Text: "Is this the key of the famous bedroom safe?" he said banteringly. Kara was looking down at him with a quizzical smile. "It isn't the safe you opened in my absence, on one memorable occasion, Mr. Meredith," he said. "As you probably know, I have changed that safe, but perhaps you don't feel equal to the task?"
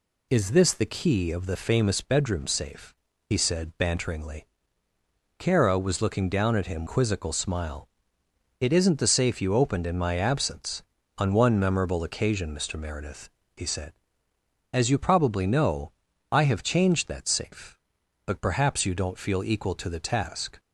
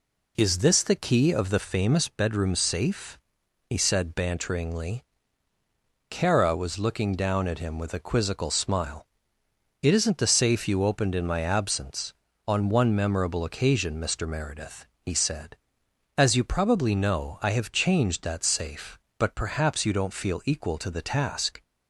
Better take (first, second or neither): second